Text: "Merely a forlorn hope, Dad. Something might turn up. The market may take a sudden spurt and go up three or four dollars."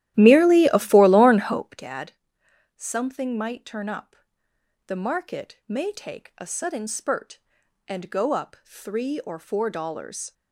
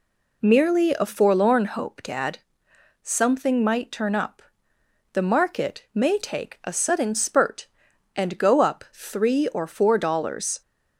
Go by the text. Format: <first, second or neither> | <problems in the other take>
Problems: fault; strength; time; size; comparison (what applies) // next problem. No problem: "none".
second | starts louder than the rest; strong; until 1.8 s; 13.5 dB